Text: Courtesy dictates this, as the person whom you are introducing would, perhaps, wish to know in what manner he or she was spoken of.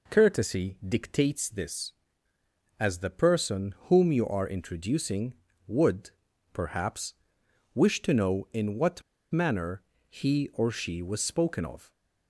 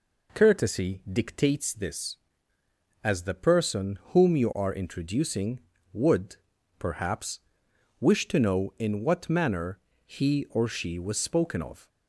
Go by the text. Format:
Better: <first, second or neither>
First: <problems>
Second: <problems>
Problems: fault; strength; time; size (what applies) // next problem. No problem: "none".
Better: second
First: pauses between "what" and "manner"; slight; at 9.0 s; 0.31 s long // pauses between "manner" and "he"; slight; at 9.8 s; 0.26 s long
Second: pauses between "manner" and "he"; slight; at 9.7 s; 0.26 s long